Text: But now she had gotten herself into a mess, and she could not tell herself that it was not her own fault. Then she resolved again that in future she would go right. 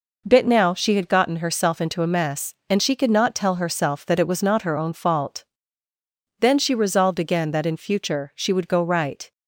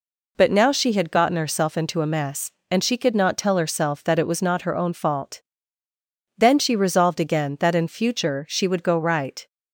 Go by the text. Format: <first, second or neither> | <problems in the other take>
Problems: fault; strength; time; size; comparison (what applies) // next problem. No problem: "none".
second | says "Bit" for "But"; at 0.2 s